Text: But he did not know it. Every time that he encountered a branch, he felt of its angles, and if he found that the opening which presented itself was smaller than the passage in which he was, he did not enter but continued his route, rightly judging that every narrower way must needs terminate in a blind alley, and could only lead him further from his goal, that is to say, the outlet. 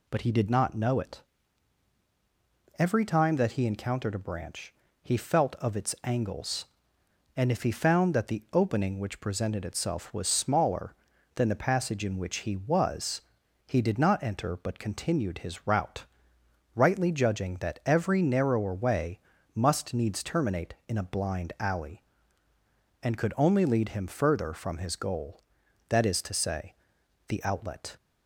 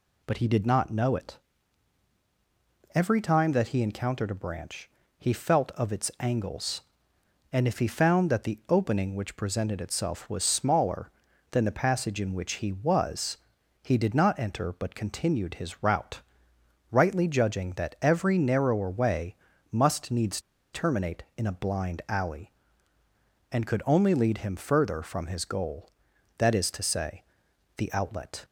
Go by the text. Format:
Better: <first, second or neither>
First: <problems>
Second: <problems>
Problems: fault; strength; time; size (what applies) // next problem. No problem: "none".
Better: first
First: pauses between "way" and "must"; slight; at 19.1 s; 0.35 s long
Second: pauses between "way" and "must"; slight; at 19.3 s; 0.36 s long // pauses between "needs" and "terminate"; slight; at 20.3 s; 0.33 s long